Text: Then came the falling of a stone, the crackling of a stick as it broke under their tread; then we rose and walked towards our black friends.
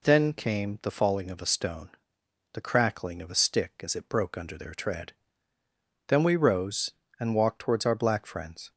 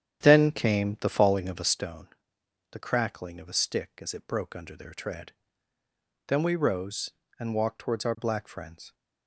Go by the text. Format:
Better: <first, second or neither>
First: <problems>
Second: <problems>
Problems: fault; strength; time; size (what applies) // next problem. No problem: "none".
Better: first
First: none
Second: starts louder than the rest; strong; until 1.8 s; 9.5 dB